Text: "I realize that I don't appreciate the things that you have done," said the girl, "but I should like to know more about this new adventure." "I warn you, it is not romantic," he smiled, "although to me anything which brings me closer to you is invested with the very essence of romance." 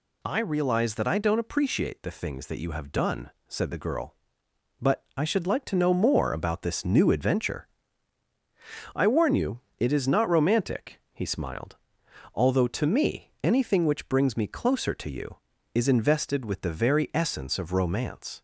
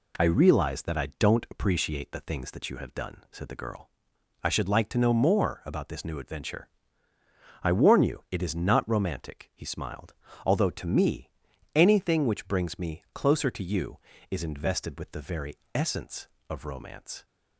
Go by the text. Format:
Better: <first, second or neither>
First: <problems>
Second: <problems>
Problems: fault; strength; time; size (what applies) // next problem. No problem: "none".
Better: first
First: none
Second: skips "but"; at 4.1 s // pauses between "me" and "anything"; noticeable; at 11.2 s; 0.46 s long // pauses between "very" and "essence"; slight; at 15.5 s; 0.16 s long